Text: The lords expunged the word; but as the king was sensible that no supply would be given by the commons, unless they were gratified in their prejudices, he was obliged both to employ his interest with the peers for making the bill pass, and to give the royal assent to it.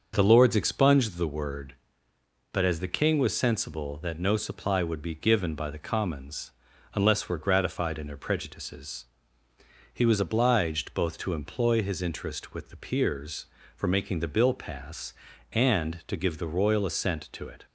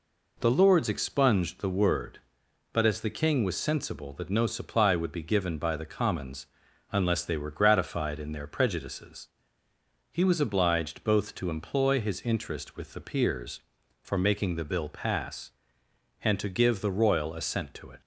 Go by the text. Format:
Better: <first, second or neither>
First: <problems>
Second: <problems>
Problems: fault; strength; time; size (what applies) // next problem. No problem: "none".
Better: second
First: starts louder than the rest; until 1.1 s; 6 dB // skips "they"; at 7.2 s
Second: none